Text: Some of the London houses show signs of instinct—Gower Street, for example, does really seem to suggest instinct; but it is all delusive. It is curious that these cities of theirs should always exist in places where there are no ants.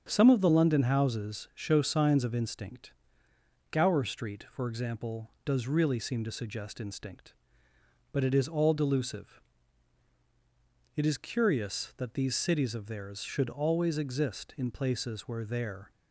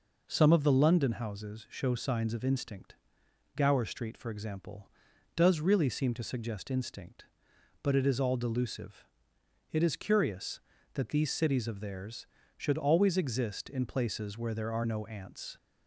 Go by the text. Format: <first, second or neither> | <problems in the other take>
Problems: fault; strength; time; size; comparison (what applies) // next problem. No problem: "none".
second | starts louder than the rest; until 1.0 s; 7 dB // stops before "are no ants"; at 15.9 s